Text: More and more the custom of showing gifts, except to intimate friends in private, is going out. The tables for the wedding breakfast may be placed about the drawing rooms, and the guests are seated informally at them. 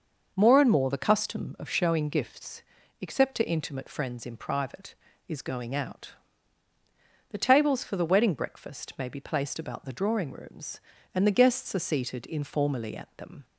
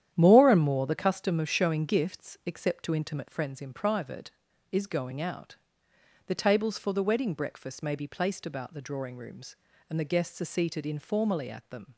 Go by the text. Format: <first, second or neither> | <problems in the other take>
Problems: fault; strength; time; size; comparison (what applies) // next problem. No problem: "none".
first | gets quieter; strong; throughout; 8.5 dB // starts louder than the rest; strong; until 1.1 s; 10 dB; noticeable in the first